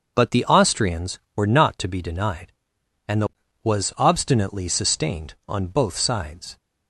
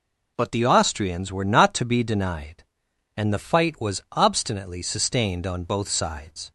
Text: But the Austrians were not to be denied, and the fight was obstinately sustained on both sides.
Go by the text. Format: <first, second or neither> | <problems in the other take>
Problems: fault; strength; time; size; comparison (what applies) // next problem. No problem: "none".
second | starts louder than the rest; until 1.1 s; 6.5 dB // skips "fight"; at 3.4 s